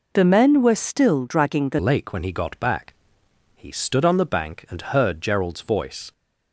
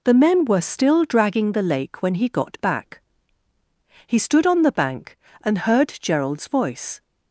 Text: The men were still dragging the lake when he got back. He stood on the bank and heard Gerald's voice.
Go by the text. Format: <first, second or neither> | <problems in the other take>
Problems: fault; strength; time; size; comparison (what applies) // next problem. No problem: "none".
second | changes voice at "lake"; from 1.7 s on; 4.4 s long